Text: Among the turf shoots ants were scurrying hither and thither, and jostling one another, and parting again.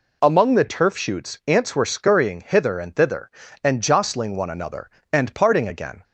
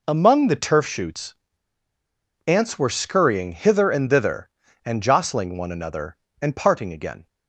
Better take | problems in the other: first | pauses between "shoots" and "ants"; at 1.3 s; 1.1 s long

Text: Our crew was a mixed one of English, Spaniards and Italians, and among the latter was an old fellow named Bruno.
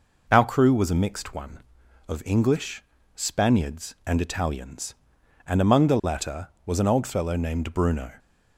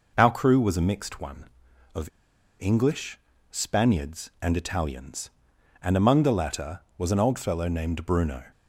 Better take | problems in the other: first | pauses between "of" and "English"; noticeable; at 2.0 s; 0.53 s long

